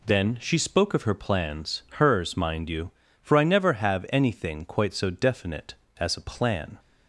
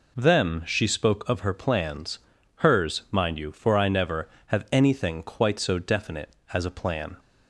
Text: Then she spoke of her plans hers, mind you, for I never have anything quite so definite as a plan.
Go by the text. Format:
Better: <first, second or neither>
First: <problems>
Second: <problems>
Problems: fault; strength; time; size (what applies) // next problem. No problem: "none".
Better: first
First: none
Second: says "Them" for "Then"; at 0.1 s // pauses between "plans" and "hers"; at 2.1 s; 0.40 s long